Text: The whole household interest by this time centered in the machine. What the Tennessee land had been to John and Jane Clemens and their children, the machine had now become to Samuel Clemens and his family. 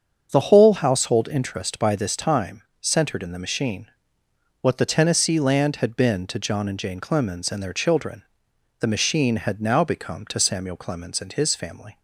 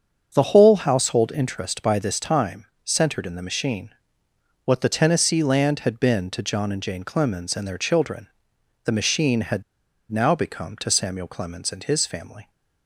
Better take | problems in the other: first | starts louder than the rest; until 1.3 s; 7 dB; also in the first // pauses between "time" and "centered"; slight; at 2.6 s; 0.18 s long; slight in the first // pauses between "had" and "now"; noticeable; at 9.6 s; 0.49 s long

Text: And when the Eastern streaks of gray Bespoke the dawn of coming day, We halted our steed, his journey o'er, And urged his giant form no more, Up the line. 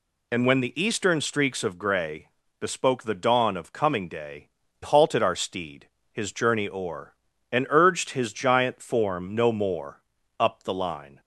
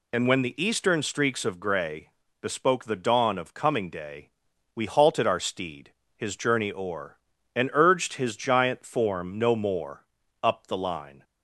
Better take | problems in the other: second | pauses between "gray" and "Bespoke"; slight; at 2.2 s; 0.30 s long; slight in the second // skips "We"; at 4.6 s

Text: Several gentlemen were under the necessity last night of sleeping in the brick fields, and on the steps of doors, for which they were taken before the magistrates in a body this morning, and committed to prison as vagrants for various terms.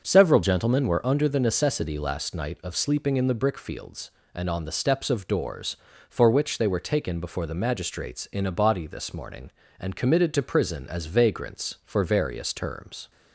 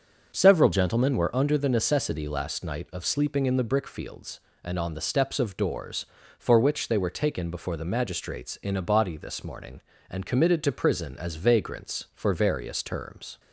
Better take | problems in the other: neither | starts louder than the rest; the same in both

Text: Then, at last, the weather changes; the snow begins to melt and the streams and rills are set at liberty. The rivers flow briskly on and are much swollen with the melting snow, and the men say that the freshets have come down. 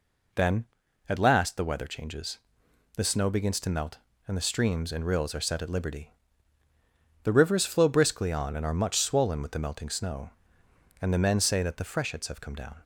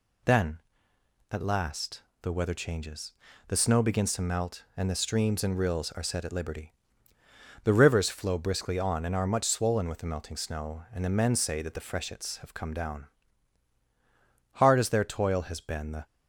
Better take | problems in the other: first | goes on to say "Hard as their toil has been the"; from 14.5 s on; 1.5 s long

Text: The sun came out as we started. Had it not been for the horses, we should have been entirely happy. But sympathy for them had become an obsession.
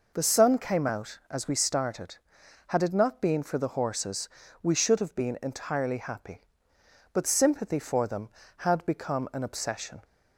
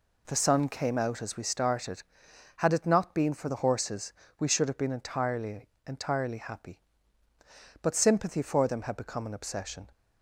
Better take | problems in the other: first | says "entirely" twice; at 5.8 s

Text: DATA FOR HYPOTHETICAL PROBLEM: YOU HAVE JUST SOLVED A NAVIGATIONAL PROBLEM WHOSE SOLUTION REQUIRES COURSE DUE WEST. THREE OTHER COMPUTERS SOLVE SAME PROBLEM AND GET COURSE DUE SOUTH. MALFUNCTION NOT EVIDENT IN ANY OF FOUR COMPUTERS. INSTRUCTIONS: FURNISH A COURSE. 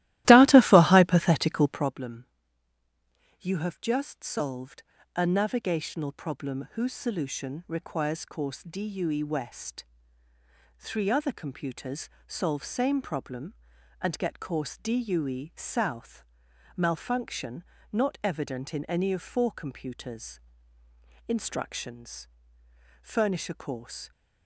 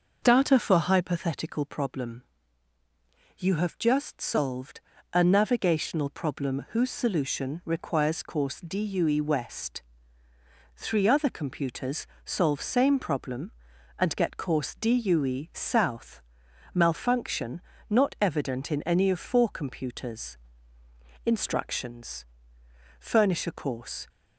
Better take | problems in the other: second | starts louder than the rest; strong; until 2.0 s; 16 dB // pauses between "SOLVED" and "A"; slight; at 4.8 s; 0.32 s long; slight in the second // pauses between "COMPUTERS" and "SOLVE"; slight; at 12.0 s; 0.16 s long; slight in the second // pauses between "MALFUNCTION" and "NOT"; slight; at 17.6 s; 0.30 s long; slight in the second

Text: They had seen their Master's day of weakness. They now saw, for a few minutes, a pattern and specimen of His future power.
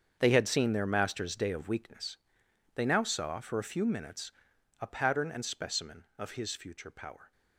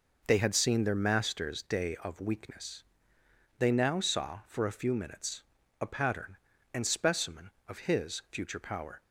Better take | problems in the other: second | gets quieter; strong; throughout; 14.5 dB

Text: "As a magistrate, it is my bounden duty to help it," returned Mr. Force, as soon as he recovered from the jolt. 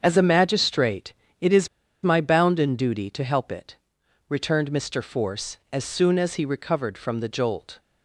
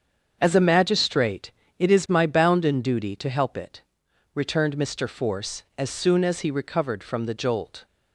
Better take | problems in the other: second | starts louder than the rest; strong; until 1.0 s; 7 dB; strong in the second // pauses between "is" and "my"; slight; at 1.6 s; 0.35 s long

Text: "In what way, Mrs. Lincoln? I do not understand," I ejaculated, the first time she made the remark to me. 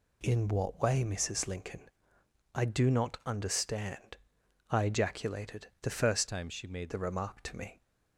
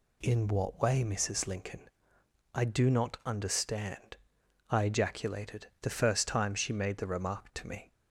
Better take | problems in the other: second | changes voice from "time" to "made"; from 6.2 to 6.9 s; 0.7 s long

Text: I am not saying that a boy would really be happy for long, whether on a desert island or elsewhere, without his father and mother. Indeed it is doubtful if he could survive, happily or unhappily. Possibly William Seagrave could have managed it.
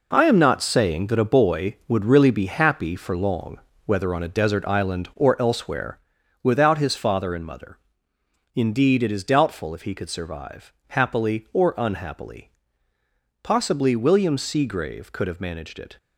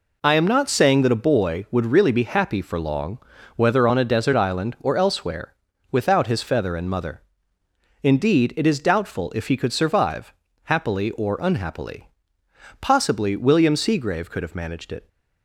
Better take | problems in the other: first | says "feather" for "father"; at 6.4 s

